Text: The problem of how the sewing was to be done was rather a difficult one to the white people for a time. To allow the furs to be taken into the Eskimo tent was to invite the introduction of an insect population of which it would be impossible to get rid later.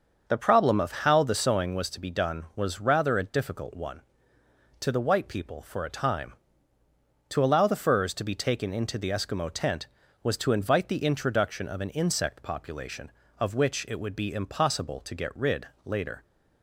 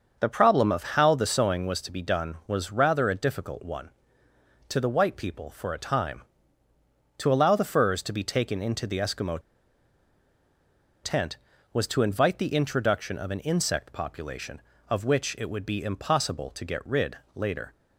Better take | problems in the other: first | starts louder than the rest; until 1.2 s; 6.5 dB; also in the first // pauses between "Eskimo" and "tent"; strong; at 9.3 s; 1.6 s long // pauses between "rid" and "later"; slight; at 17.1 s; 0.16 s long; slight in the first

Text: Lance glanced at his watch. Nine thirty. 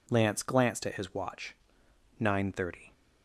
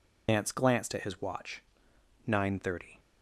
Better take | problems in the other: first | loses the start of "Lance"; at 0.2 s; 105 ms

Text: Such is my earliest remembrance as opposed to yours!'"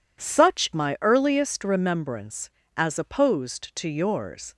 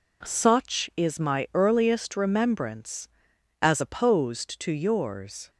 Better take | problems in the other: second | skips "is"; at 0.7 s

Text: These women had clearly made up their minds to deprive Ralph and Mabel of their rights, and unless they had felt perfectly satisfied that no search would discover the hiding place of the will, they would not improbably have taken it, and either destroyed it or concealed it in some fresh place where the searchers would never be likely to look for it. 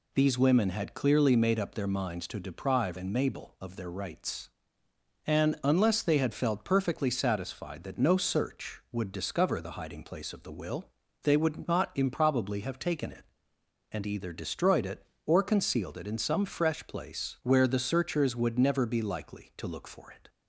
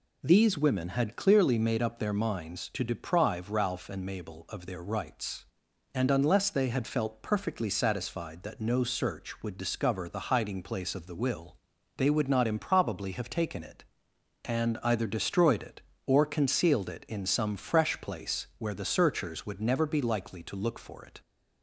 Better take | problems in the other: second | skips "Ralph"; at 2.9 s

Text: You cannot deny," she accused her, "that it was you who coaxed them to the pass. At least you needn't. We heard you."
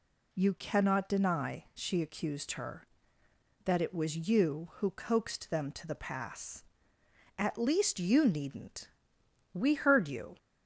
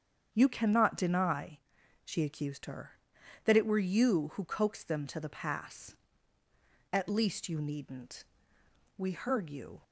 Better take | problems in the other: first | starts louder than the rest; strong; until 1.3 s; 7.5 dB // says "were" for "was"; at 3.6 s

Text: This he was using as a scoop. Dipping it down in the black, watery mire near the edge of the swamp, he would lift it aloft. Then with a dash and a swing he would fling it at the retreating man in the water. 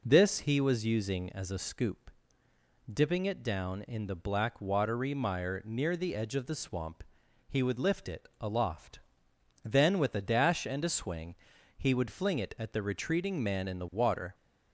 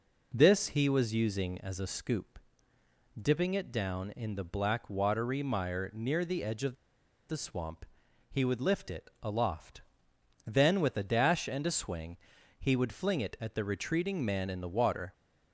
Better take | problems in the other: first | pauses between "of" and "the"; noticeable; at 6.7 s; 0.56 s long // pauses between "swing" and "he"; at 12.1 s; 0.44 s long; also in the first

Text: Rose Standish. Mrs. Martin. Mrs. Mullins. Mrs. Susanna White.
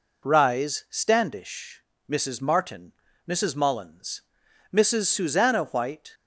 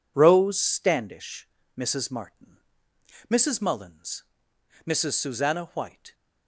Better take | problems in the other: second | says "Rise" for "Rose"; at 0.2 s

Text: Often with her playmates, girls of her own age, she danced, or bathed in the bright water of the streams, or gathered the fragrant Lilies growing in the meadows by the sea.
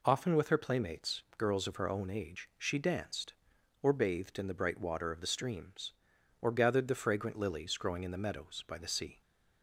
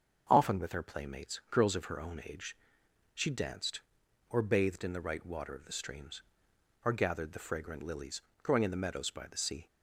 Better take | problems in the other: first | starts louder than the rest; until 1.3 s; 7 dB // says "right" for "bright"; at 4.9 s // pauses between "Lilies" and "growing"; slight; at 8.1 s; 0.22 s long

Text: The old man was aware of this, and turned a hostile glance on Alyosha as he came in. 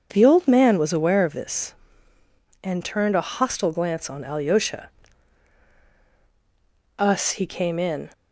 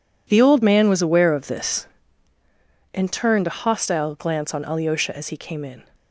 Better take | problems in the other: second | says "us" for "as"; at 6.9 s

